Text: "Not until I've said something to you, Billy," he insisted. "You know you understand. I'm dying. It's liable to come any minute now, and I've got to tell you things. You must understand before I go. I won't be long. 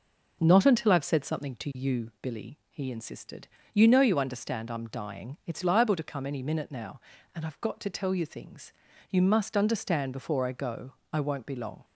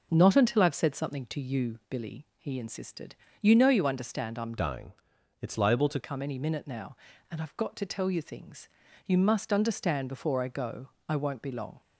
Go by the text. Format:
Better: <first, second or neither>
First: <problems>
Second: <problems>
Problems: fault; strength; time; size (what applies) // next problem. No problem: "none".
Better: first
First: none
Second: changes voice from "dying" to "to"; from 4.5 to 5.9 s; 1.4 s long